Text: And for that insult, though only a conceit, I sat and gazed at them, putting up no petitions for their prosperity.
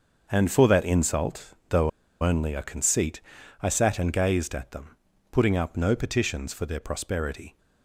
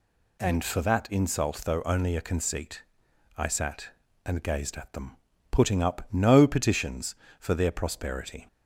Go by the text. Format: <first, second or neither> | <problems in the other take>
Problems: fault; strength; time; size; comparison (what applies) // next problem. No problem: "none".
second | starts louder than the rest; until 1.3 s; 6.5 dB // pauses between "though" and "only"; slight; at 1.8 s; 0.33 s long